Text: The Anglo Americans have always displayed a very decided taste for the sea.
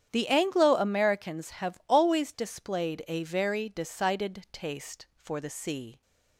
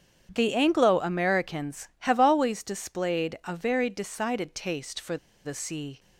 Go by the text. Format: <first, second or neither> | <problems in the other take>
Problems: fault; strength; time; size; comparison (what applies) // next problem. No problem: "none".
first | starts louder than the rest; strong; until 1.3 s; 8 dB; strong in the first // pauses between "for" and "the"; slight; at 5.1 s; 0.28 s long